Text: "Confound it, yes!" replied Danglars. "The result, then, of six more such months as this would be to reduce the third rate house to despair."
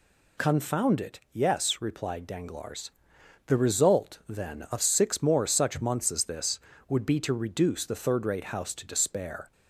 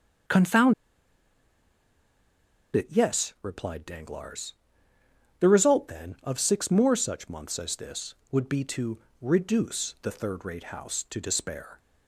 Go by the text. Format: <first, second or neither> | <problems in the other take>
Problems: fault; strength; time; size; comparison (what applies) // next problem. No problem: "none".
first | starts louder than the rest; until 3.3 s; 7 dB // pauses between "Confound" and "it"; strong; at 0.7 s; 2.0 s long // pauses between "to" and "reduce"; slight; at 8.9 s; 0.22 s long